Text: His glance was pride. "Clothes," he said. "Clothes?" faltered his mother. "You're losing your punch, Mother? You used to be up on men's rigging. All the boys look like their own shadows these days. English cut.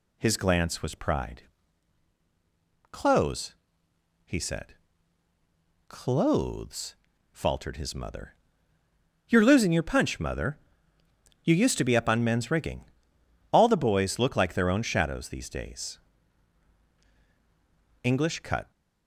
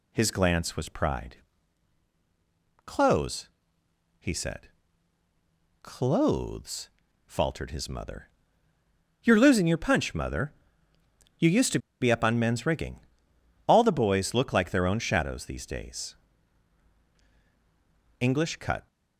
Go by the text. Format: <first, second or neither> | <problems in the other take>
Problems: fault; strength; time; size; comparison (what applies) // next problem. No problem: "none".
first | pauses between "to" and "be"; slight; at 11.7 s; 0.22 s long